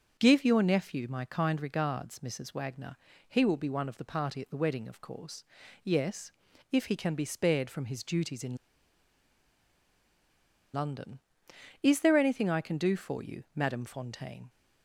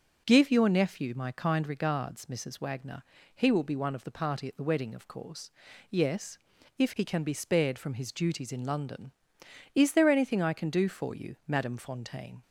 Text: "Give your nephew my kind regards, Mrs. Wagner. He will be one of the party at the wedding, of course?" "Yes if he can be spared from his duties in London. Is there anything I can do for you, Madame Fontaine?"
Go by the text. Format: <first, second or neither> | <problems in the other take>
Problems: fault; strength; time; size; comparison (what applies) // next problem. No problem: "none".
second | pauses between "Yes" and "if"; at 6.3 s; 0.40 s long; also in the second // pauses between "in" and "London"; strong; at 8.5 s; 2.1 s long